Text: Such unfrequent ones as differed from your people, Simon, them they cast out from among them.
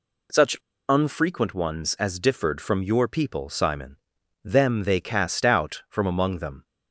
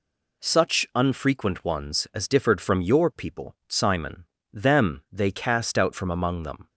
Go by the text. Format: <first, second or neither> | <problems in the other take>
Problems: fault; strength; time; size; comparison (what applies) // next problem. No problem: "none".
second | pauses between "Such" and "unfrequent"; slight; at 0.5 s; 0.34 s long